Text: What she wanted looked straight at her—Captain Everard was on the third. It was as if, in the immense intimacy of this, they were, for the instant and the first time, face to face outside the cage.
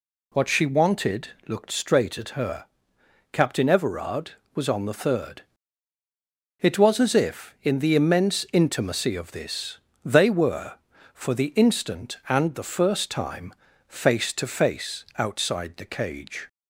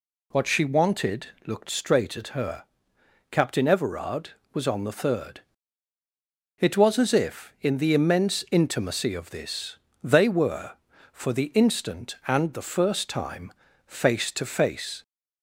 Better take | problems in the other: first | pauses between "wanted" and "looked"; slight; at 1.2 s; 0.18 s long; slight in the first // stops before "outside the cage"; at 15.0 s

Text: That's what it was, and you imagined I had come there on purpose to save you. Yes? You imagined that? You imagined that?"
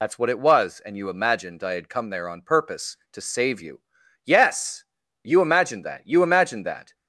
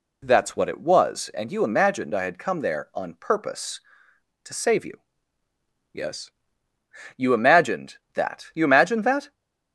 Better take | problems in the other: second | loses the start of "That's"; at 0.0 s; 70 ms

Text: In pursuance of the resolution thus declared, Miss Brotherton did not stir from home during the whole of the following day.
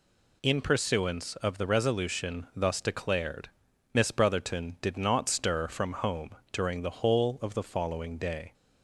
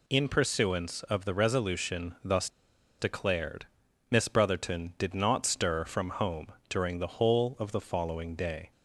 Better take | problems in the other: first | pauses between "thus" and "declared"; noticeable; at 2.4 s; 0.51 s long // pauses between "home" and "during"; slight; at 6.4 s; 0.22 s long; slight in the first

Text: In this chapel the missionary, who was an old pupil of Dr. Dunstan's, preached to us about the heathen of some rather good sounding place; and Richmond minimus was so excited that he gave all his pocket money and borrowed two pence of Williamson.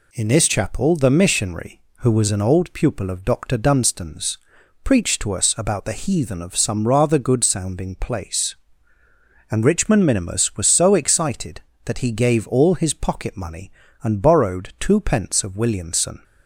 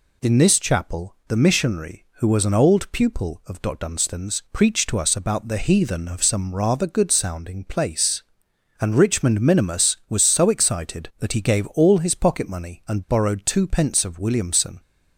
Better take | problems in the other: neither | none

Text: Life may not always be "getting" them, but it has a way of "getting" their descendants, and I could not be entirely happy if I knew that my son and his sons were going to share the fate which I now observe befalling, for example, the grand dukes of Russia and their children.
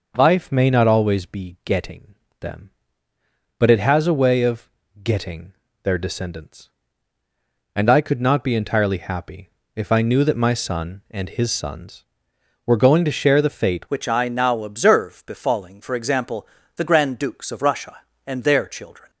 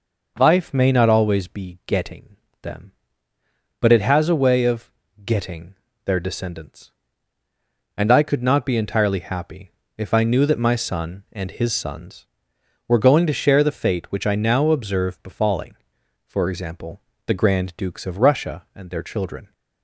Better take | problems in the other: second | pauses between "getting" and "them"; slight; at 2.1 s; 0.26 s long; slight in the second // pauses between "of" and "getting"; slight; at 4.7 s; 0.32 s long; slight in the second // pauses between "getting" and "their"; slight; at 5.5 s; 0.30 s long; slight in the second // pauses between "happy" and "if"; slight; at 9.4 s; 0.26 s long; slight in the second // changes voice at "which"; from 13.8 s on; 5.2 s long

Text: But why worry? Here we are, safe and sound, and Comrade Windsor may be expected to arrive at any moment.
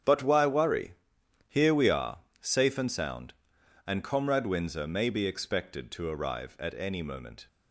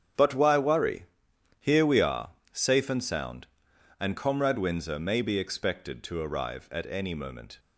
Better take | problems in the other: neither | starts louder than the rest; strong; the same in both

